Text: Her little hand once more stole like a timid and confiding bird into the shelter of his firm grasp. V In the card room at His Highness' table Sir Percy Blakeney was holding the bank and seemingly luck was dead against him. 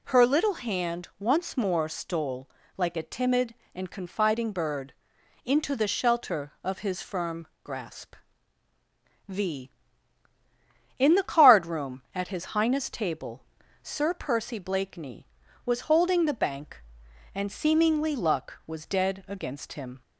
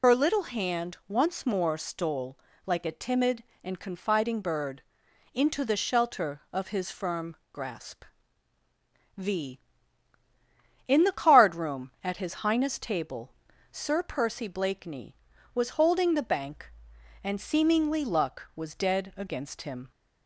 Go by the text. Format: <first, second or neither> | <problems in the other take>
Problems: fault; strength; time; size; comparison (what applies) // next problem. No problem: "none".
first | loses the start of "Her"; at 0.0 s; 80 ms // pauses between "stole" and "like"; slight; at 2.3 s; 0.30 s long; slight in the first // pauses between "bird" and "into"; noticeable; at 4.8 s; 0.50 s long; noticeable in the first // pauses between "firm" and "grasp"; slight; at 7.3 s; 0.16 s long; slight in the first // pauses between "table" and "Sir"; at 13.3 s; 0.40 s long; also in the first